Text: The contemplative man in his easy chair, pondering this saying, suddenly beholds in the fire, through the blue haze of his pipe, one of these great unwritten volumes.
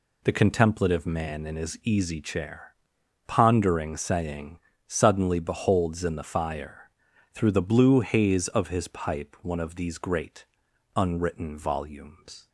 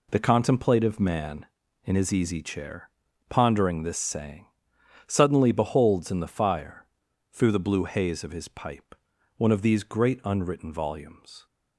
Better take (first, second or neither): second